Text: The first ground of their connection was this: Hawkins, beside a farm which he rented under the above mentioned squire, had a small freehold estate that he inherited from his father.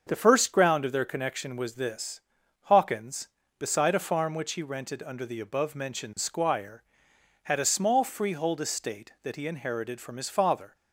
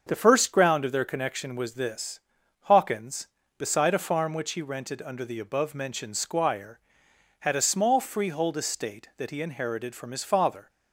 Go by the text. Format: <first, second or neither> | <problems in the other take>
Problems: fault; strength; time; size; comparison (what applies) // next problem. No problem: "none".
neither | starts louder than the rest; the same in both